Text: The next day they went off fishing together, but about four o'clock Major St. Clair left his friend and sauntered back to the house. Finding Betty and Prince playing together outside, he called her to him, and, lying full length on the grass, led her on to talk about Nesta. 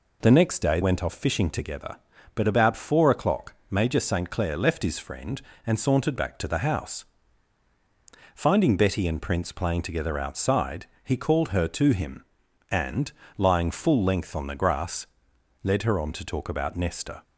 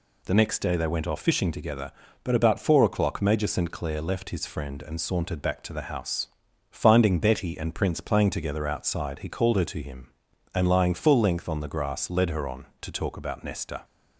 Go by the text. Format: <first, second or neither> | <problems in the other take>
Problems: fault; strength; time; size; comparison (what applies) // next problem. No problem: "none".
second | skips "they"; at 0.8 s // pauses between "o'clock" and "Major"; slight; at 3.5 s; 0.16 s long